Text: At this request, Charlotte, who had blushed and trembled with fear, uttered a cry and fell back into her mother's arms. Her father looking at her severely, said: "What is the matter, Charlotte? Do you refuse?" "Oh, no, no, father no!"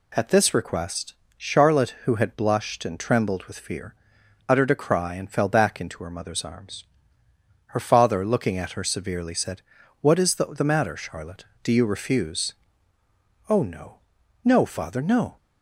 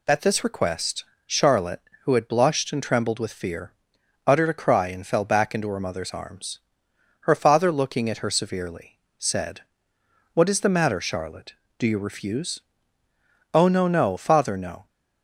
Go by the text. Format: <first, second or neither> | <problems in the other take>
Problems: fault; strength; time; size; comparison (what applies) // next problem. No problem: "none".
second | says "the" twice; at 10.4 s